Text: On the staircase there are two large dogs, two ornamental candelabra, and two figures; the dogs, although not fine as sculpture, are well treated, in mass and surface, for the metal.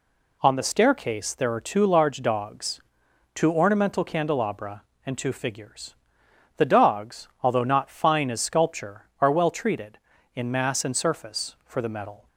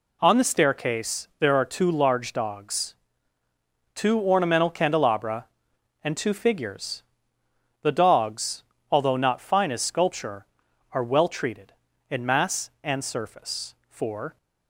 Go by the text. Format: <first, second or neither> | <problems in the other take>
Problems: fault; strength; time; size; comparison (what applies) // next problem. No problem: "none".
first | stops before "the metal"; at 14.3 s